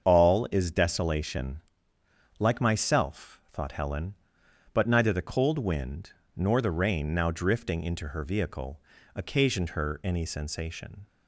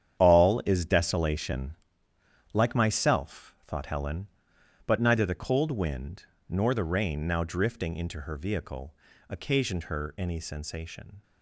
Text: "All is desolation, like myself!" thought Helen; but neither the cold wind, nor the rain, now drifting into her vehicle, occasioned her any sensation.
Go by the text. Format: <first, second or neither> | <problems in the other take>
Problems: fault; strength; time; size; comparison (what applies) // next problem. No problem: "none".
first | gets quieter; strong; throughout; 11.5 dB // starts louder than the rest; strong; until 1.2 s; 9 dB; also in the first